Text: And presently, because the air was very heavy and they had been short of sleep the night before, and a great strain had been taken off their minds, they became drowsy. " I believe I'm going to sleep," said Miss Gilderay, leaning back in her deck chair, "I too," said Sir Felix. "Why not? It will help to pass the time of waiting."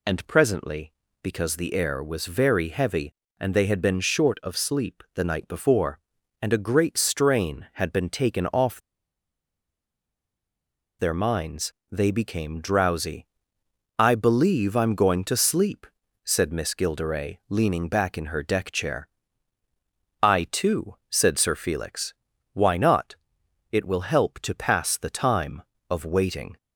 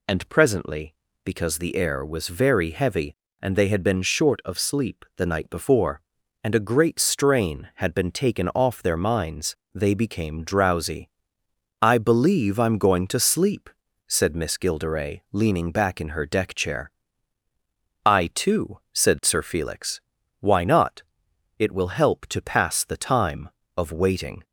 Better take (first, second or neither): second